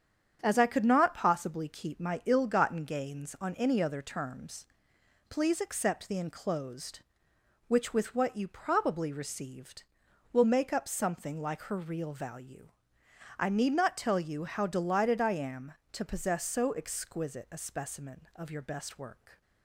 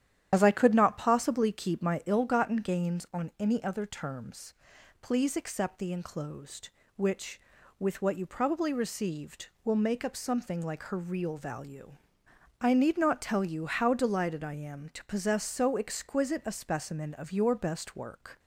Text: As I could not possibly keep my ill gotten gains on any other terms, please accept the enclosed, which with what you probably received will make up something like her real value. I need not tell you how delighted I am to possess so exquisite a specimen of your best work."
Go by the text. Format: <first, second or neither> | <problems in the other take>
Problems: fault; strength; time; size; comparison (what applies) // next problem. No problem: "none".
first | loses the start of "As"; at 0.3 s; 45 ms // starts louder than the rest; strong; until 1.3 s; 10.5 dB; strong in the first